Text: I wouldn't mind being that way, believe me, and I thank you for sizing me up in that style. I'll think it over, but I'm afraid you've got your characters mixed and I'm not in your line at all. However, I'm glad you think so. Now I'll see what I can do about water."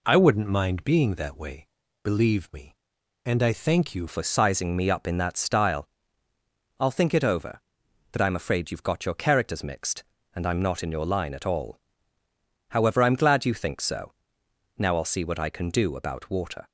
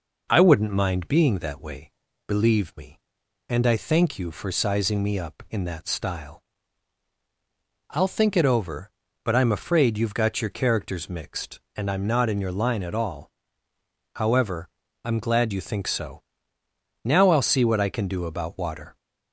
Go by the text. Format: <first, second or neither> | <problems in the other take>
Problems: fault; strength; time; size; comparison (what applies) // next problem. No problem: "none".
second | changes voice at "for"; from 4.0 s on; 12.6 s long